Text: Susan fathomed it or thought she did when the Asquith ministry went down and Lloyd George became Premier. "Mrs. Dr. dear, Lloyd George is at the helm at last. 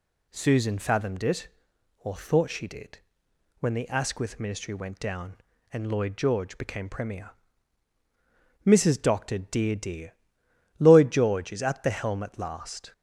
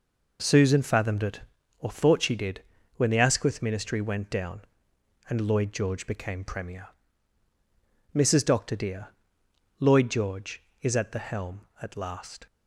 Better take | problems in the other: second | pauses between "did" and "when"; noticeable; at 2.9 s; 0.62 s long; slight in the second // says "dear" twice; at 9.7 s

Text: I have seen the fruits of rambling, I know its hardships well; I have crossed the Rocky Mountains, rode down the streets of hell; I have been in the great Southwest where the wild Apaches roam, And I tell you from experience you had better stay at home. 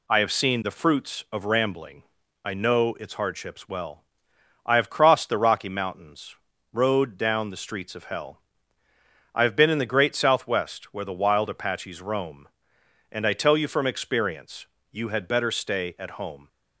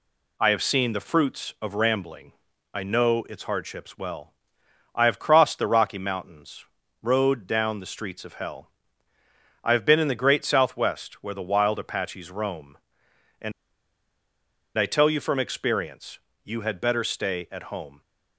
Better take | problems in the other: first | pauses between "And" and "I"; strong; at 13.5 s; 1.2 s long // pauses between "experience" and "you"; slight; at 16.1 s; 0.26 s long; slight in the first

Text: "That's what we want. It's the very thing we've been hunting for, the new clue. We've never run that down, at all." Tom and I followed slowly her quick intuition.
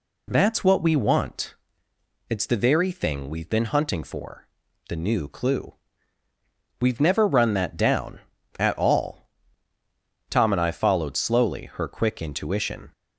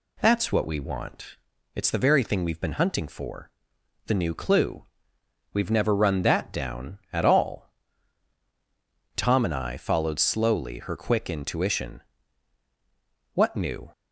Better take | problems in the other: first | goes on to say "What new"; from 13.3 s on; 0.56 s long

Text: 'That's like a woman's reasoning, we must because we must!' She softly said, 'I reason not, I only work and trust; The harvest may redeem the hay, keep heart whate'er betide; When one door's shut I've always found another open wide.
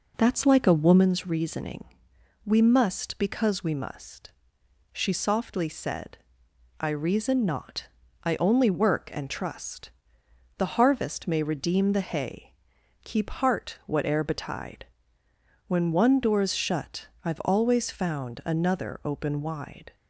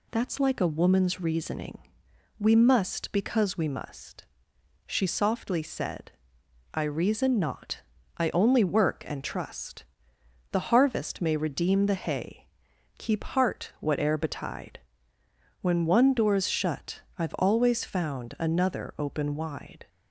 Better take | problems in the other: second | starts louder than the rest; noticeable; until 1.1 s; 4 dB // pauses between "shut" and "I've"; slight; at 17.0 s; 0.16 s long; slight in the second

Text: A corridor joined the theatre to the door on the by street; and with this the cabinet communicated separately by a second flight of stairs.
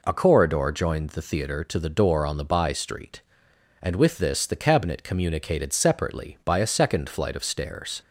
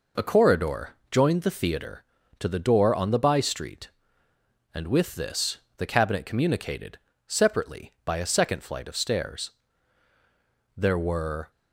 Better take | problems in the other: first | pauses between "corridor" and "joined"; slight; at 0.9 s; 0.16 s long // pauses between "this" and "the"; slight; at 5.5 s; 0.18 s long // pauses between "communicated" and "separately"; slight; at 6.9 s; 0.28 s long // goes on to say "There were"; noticeable; from 10.7 s on; 0.76 s long

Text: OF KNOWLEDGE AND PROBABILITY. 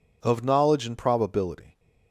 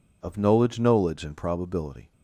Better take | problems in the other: first | says "KNOWLEDGE" twice; at 0.7 s

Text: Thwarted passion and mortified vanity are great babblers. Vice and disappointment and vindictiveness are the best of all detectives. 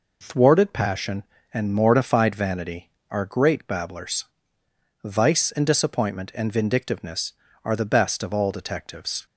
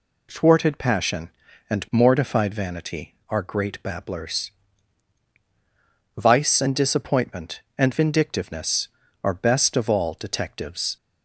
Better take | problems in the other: first | skips "the"; at 9.3 s

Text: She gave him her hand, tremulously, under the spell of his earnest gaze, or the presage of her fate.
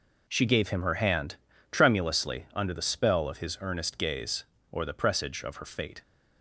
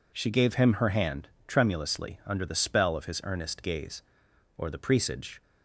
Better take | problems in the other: first | stops before "of her fate"; at 5.4 s

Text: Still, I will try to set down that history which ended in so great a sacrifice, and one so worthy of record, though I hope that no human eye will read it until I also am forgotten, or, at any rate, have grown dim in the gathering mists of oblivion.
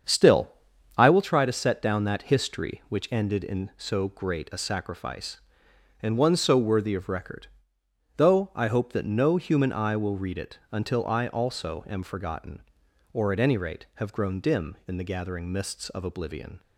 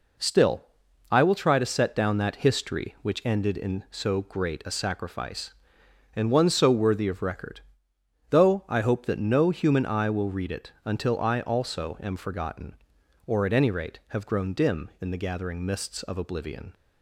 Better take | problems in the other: second | starts louder than the rest; strong; until 1.3 s; 7.5 dB

